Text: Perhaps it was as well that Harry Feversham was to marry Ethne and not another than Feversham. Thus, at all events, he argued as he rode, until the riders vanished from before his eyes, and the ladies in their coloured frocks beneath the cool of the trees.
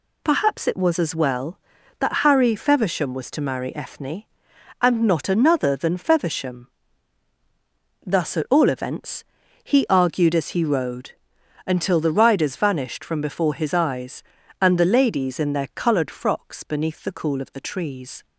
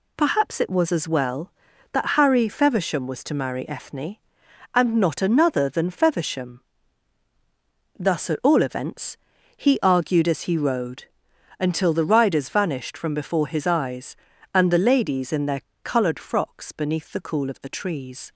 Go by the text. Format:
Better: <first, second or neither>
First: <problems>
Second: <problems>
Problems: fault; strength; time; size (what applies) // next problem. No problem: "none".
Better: first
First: none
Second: pauses between "their" and "coloured"; slight; at 15.6 s; 0.21 s long